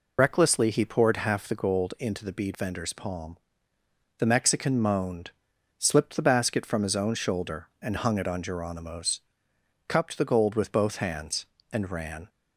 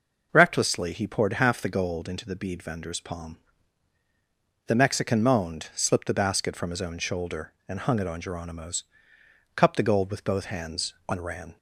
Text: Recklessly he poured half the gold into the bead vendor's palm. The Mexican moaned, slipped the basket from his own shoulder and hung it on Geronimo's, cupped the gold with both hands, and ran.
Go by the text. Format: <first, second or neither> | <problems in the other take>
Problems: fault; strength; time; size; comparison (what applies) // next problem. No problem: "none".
second | loses the start of "Recklessly"; at 0.1 s; 40 ms